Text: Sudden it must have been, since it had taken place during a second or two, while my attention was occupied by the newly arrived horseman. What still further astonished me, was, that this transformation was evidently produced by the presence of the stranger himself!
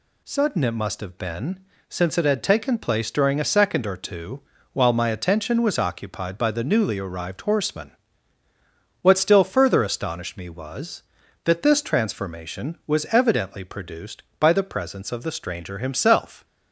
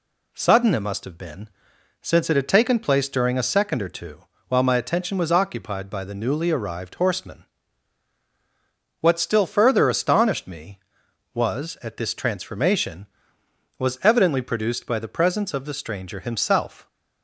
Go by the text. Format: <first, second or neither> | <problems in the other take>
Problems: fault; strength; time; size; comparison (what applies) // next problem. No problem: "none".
first | says "at" for "that"; at 11.8 s